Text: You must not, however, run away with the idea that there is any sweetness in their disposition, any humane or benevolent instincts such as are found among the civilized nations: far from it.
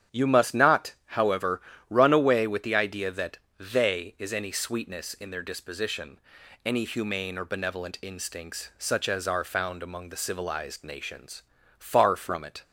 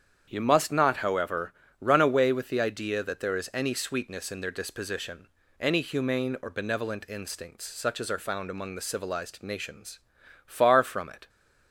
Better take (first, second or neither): second